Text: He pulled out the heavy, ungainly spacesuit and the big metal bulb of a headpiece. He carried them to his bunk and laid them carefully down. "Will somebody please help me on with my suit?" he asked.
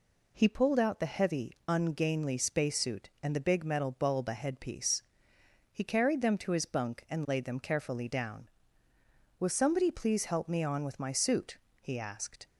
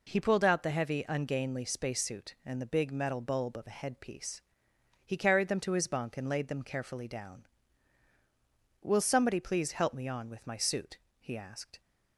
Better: second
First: skips "of"; at 4.2 s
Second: none

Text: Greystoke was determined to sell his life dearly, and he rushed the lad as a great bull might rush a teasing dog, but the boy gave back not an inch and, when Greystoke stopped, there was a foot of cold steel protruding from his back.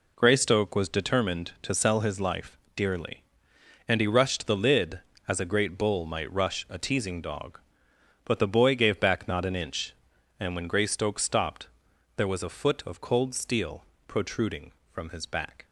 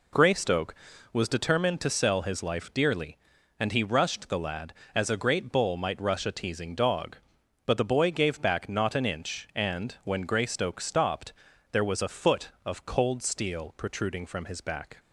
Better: second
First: pauses between "life" and "dearly"; slight; at 2.5 s; 0.20 s long // says "lid" for "lad"; at 4.5 s // pauses between "steel" and "protruding"; slight; at 13.8 s; 0.22 s long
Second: none

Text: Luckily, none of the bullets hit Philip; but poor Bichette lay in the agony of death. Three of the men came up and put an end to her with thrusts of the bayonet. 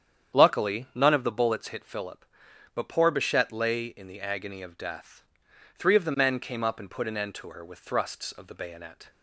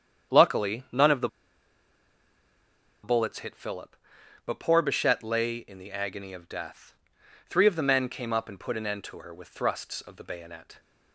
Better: first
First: starts louder than the rest; strong; until 1.4 s; 8.5 dB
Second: starts louder than the rest; strong; until 3.1 s; 8.5 dB // pauses between "the" and "bullets"; strong; at 1.2 s; 1.7 s long

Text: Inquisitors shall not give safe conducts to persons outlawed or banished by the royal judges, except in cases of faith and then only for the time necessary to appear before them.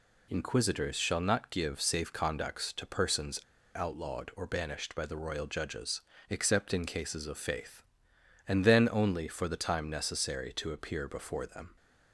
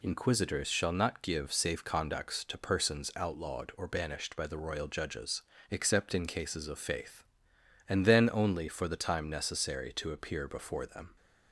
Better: second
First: pauses between "persons" and "outlawed"; slight; at 3.4 s; 0.33 s long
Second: none

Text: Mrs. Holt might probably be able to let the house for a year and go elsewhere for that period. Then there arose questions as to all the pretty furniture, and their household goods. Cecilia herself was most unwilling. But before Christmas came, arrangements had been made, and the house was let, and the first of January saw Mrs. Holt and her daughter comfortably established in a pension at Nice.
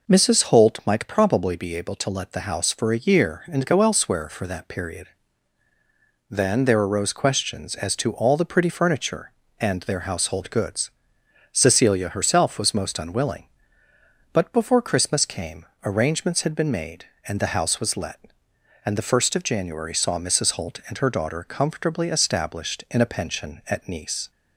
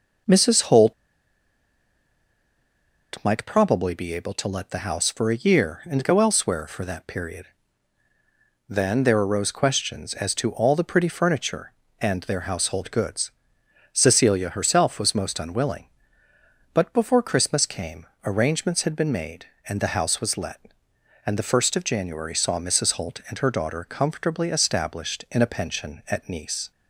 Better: first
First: none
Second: pauses between "Holt" and "might"; strong; at 0.9 s; 2.2 s long

